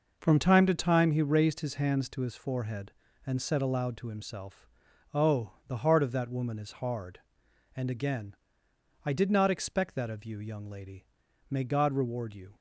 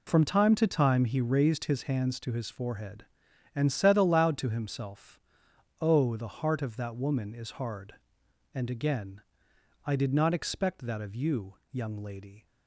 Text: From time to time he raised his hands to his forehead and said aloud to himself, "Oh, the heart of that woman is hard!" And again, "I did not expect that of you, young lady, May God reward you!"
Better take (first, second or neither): first